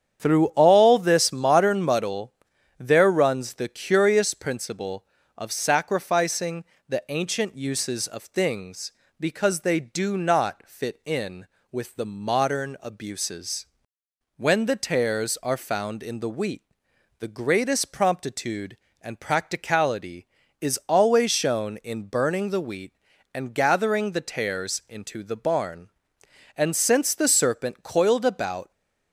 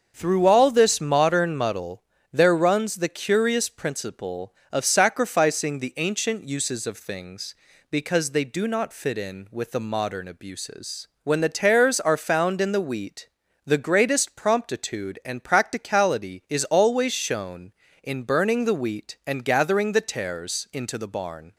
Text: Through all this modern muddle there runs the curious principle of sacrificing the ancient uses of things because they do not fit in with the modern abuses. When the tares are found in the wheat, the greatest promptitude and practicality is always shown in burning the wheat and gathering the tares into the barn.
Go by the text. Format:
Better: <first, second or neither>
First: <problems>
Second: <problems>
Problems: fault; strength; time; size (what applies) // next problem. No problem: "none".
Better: second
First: starts louder than the rest; strong; until 1.2 s; 8.5 dB // pauses between "muddle" and "there"; at 2.3 s; 0.42 s long // pauses between "sacrificing" and "the"; slight; at 6.6 s; 0.24 s long // goes on to say "And since the serpent coiled about"; strong; from 26.5 s on; 2.1 s long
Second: starts louder than the rest; until 1.1 s; 6.5 dB // pauses between "muddle" and "there"; slight; at 2.0 s; 0.30 s long